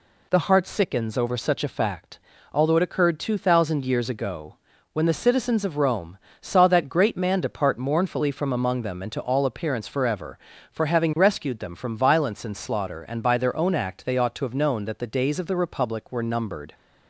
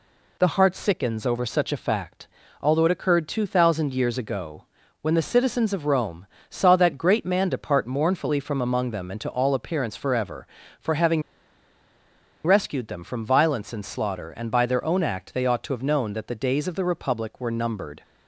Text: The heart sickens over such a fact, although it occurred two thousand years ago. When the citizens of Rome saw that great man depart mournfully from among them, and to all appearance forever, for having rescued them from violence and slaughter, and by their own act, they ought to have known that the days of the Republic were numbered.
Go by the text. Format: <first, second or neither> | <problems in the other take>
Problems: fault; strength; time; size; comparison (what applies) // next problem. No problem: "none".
first | pauses between "Rome" and "saw"; slight; at 6.2 s; 0.24 s long; slight in the first // pauses between "having" and "rescued"; at 11.2 s; 1.2 s long